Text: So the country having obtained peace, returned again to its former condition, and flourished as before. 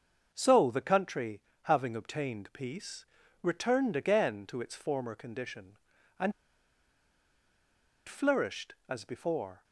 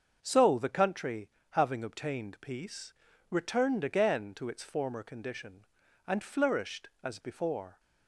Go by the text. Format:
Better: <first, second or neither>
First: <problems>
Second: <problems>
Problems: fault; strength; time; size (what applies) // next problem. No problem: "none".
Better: second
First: starts louder than the rest; until 1.3 s; 6.5 dB // pauses between "country" and "having"; slight; at 1.4 s; 0.20 s long // pauses between "and" and "flourished"; strong; at 6.3 s; 1.7 s long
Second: starts louder than the rest; until 1.2 s; 6.5 dB // pauses between "country" and "having"; slight; at 1.3 s; 0.20 s long